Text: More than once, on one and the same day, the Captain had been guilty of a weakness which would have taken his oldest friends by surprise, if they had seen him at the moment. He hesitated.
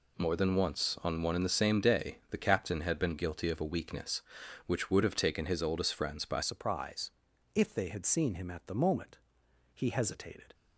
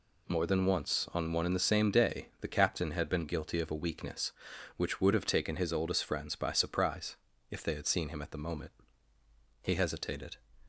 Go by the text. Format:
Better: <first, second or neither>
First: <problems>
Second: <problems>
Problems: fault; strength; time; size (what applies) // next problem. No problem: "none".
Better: second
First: changes voice at "surprise"; from 6.4 s on; 4.1 s long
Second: none